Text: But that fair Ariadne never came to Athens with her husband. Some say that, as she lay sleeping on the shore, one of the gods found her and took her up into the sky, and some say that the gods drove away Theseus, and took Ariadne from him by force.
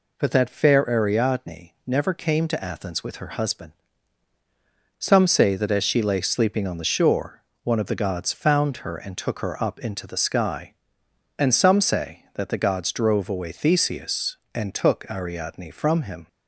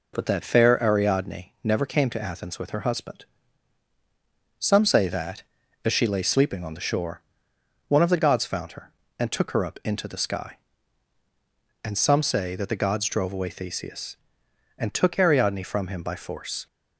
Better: second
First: stops before "by force"; at 16.2 s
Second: none

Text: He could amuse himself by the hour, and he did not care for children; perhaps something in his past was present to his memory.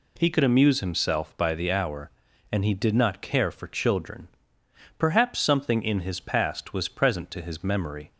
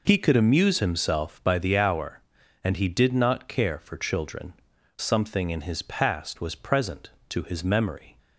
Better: first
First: none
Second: skips "perhaps"; at 4.7 s

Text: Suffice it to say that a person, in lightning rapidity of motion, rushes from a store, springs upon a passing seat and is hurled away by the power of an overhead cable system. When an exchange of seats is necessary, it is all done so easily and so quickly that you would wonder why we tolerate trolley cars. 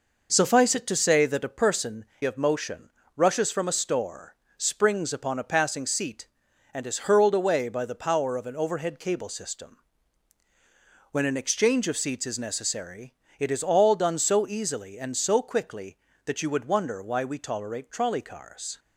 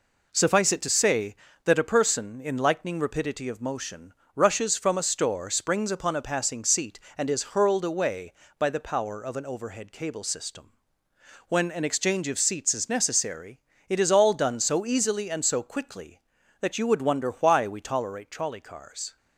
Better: second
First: skips "in lightning rapidity"; at 2.1 s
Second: none

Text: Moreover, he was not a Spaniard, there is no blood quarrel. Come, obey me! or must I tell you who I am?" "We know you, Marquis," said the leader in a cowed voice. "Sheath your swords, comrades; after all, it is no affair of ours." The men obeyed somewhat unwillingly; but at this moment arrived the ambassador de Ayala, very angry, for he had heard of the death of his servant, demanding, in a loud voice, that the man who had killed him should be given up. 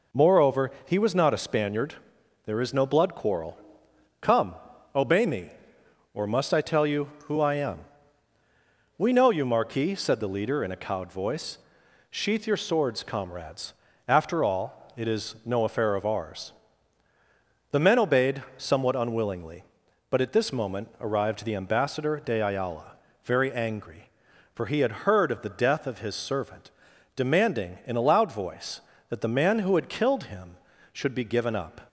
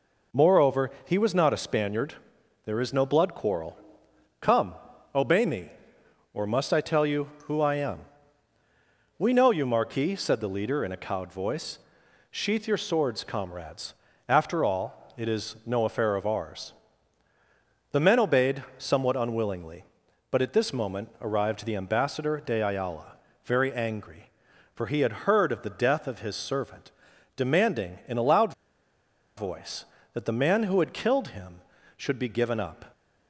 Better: first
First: none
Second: pauses between "loud" and "voice"; noticeable; at 28.5 s; 0.84 s long

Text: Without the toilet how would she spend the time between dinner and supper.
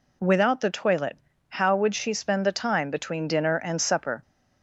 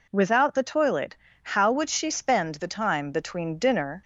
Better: first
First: pauses between "toilet" and "how"; slight; at 1.1 s; 0.32 s long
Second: pauses between "toilet" and "how"; slight; at 1.1 s; 0.28 s long // stops before "and supper"; at 4.0 s

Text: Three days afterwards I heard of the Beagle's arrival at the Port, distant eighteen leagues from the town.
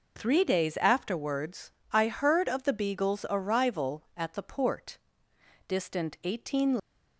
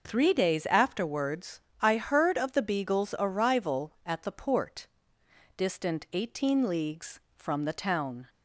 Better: second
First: pauses between "afterwards" and "I"; slight; at 1.7 s; 0.22 s long // stops before "leagues from the town"; at 6.7 s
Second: pauses between "afterwards" and "I"; slight; at 1.6 s; 0.22 s long

